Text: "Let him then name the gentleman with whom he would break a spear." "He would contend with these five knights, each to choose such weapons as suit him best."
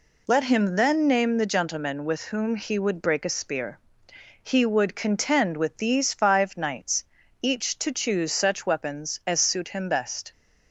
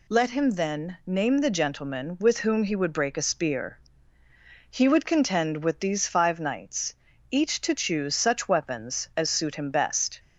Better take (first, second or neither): neither